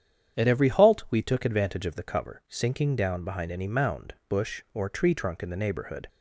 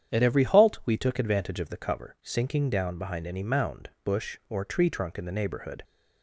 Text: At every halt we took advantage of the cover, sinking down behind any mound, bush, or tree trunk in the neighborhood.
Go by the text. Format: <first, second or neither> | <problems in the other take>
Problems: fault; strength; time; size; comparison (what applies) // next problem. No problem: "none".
neither | starts louder than the rest; strong; the same in both